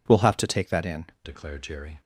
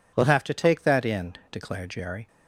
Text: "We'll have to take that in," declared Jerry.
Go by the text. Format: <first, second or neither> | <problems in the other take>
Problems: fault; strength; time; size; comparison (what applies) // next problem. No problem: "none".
second | changes voice at "declared"; from 1.2 s on; 0.8 s long